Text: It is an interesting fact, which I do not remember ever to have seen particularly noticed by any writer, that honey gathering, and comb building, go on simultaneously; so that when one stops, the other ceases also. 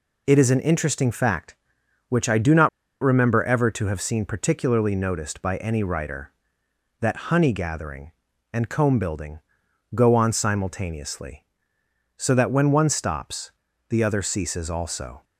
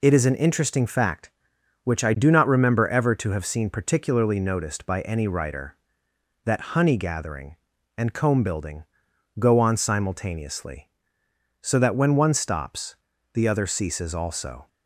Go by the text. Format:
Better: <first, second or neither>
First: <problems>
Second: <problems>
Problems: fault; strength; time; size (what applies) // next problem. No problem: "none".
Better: second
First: pauses between "not" and "remember"; slight; at 2.6 s; 0.32 s long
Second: none